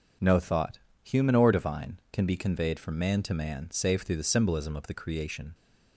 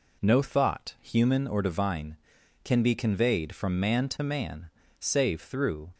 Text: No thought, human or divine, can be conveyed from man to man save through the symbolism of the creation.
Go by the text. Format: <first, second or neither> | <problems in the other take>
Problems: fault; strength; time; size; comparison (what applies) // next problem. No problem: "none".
first | pauses between "man" and "save"; slight; at 4.6 s; 0.30 s long // stops before "the symbolism of the creation"; at 5.9 s